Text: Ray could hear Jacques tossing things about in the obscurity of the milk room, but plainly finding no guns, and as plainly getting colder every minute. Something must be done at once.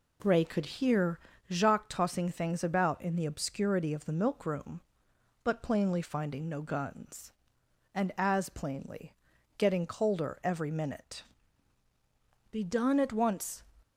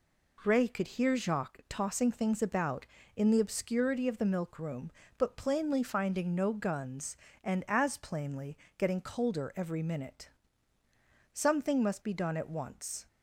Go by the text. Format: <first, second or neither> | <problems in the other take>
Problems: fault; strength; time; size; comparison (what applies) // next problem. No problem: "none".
second | pauses between "hear" and "Jacques"; slight; at 1.1 s; 0.32 s long // pauses between "plainly" and "getting"; at 9.1 s; 0.44 s long; slight in the second // skips "Something must"; at 11.8 s